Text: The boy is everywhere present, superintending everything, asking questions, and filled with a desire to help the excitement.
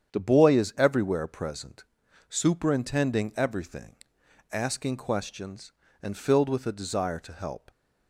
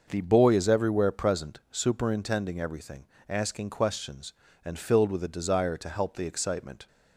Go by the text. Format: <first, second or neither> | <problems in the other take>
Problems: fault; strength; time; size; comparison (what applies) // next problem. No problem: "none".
second | starts louder than the rest; strong; until 1.1 s; 8 dB; also in the second // stops before "the excitement"; at 7.6 s